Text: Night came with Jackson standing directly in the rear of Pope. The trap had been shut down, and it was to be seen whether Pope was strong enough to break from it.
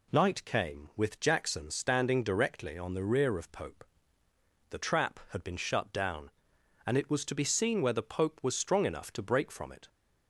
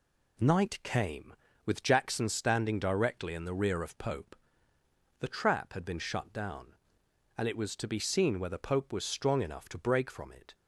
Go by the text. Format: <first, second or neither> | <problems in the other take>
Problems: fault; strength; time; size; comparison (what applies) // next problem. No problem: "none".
second | says "on" for "in"; at 2.7 s